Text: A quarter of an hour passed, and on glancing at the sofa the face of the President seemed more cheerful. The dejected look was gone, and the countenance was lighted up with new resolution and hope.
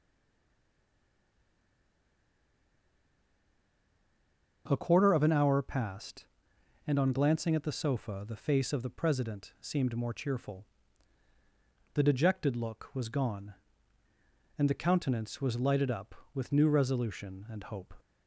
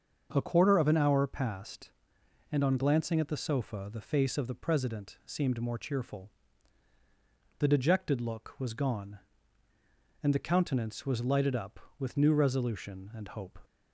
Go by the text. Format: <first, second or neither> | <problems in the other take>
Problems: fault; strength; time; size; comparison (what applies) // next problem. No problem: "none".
second | stays silent before the first word; strong; until 4.6 s; 4.6 s long // starts louder than the rest; until 5.6 s; 6.5 dB; also in the second